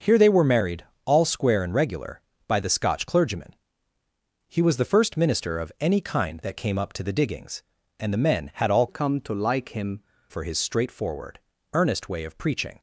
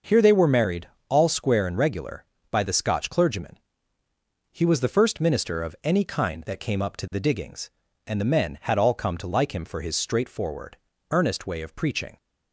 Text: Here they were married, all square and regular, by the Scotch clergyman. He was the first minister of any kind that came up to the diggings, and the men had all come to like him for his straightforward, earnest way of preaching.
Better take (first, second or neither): second